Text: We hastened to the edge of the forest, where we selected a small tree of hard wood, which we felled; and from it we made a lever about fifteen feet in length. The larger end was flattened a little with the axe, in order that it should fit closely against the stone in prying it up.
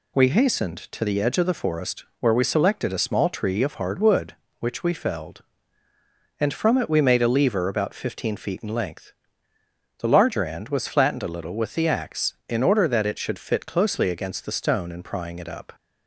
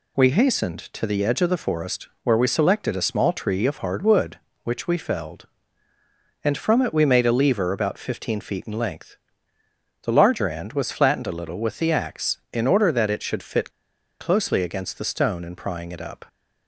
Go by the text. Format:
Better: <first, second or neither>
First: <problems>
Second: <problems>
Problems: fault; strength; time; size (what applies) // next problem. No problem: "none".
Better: first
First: none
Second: pauses between "fit" and "closely"; noticeable; at 13.6 s; 0.51 s long